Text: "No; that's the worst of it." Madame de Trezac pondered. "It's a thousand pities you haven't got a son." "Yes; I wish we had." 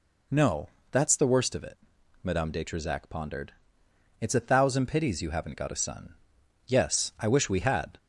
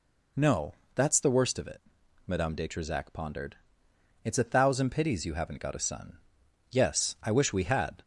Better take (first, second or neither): neither